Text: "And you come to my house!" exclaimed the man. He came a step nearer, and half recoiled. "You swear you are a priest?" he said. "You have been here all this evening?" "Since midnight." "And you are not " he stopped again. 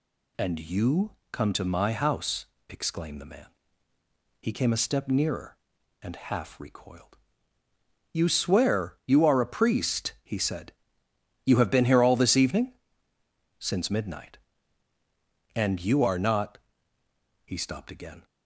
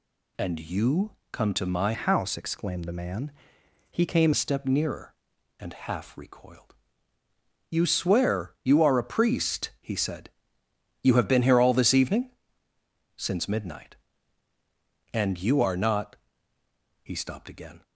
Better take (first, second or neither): first